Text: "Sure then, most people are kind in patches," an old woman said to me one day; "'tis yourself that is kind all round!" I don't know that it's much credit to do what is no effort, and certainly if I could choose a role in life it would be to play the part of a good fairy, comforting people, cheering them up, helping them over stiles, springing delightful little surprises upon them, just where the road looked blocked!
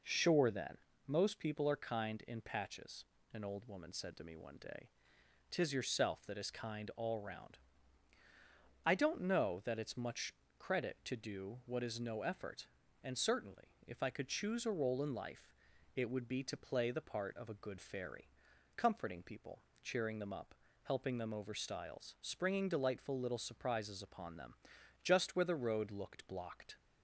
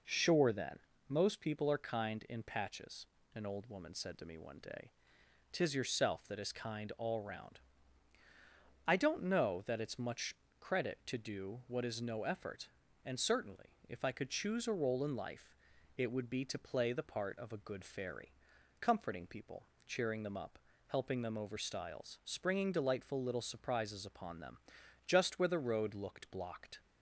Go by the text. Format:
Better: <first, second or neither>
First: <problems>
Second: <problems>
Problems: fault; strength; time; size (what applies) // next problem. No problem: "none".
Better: neither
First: pauses between "much" and "credit"; slight; at 10.3 s; 0.24 s long // pauses between "life" and "it"; at 15.5 s; 0.40 s long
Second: pauses between "much" and "credit"; slight; at 10.3 s; 0.24 s long // pauses between "life" and "it"; at 15.5 s; 0.40 s long